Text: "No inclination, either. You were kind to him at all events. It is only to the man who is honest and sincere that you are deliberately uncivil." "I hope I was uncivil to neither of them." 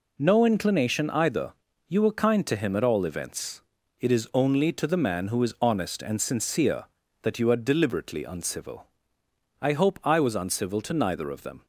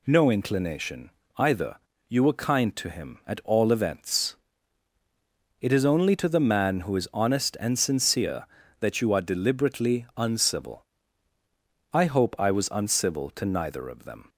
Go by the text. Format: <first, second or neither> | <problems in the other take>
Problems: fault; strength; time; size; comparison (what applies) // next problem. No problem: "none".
neither | none